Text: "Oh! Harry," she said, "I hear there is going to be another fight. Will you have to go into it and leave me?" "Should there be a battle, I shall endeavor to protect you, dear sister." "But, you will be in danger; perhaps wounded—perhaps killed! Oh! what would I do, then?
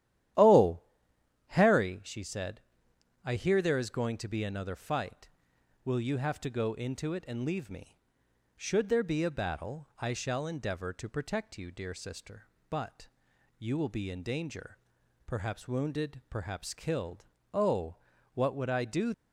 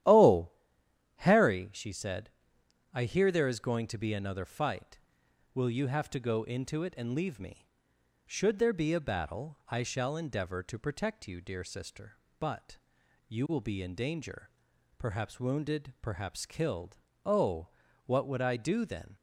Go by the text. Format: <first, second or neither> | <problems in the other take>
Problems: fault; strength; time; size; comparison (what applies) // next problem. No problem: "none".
second | starts louder than the rest; strong; until 2.1 s; 12 dB; strong in the second // stops before "then"; at 19.1 s